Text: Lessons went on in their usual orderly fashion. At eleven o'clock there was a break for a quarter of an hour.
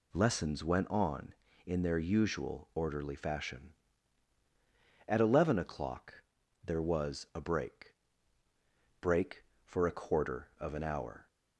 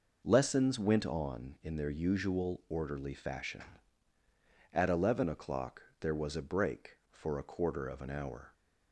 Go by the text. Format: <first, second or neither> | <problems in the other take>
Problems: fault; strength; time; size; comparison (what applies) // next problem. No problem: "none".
second | pauses between "o'clock" and "there"; at 6.2 s; 0.42 s long; slight in the second // says "break" twice; at 8.9 s